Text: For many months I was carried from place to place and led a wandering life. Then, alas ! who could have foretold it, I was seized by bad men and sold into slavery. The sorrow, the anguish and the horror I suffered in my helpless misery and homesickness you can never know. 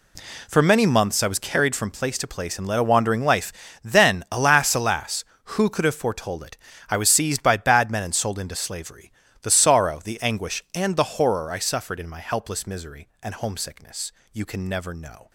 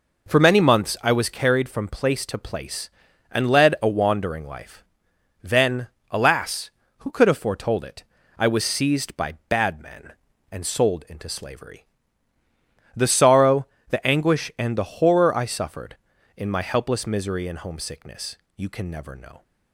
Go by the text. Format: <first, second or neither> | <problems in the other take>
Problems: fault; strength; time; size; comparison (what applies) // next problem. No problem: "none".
second | says "alas" twice; at 4.7 s // pauses between "homesickness" and "you"; slight; at 14.1 s; 0.22 s long; slight in the second